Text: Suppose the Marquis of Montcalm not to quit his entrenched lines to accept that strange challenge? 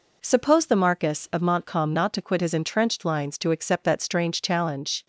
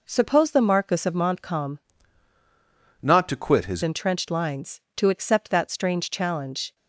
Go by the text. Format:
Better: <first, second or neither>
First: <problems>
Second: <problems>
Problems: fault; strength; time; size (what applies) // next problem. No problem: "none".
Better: first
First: none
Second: changes voice from "not" to "his"; from 3.0 to 3.8 s; 0.8 s long